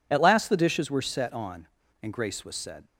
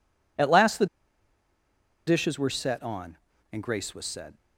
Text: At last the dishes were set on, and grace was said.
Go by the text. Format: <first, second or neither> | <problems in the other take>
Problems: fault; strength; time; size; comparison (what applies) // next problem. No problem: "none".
first | pauses between "the" and "dishes"; at 0.8 s; 1.2 s long